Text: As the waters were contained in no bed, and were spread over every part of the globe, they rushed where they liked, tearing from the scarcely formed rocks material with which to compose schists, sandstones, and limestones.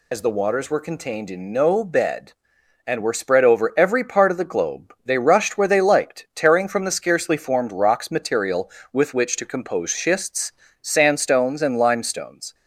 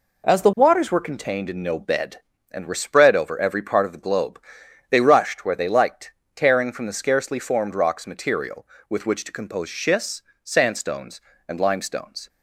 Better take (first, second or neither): second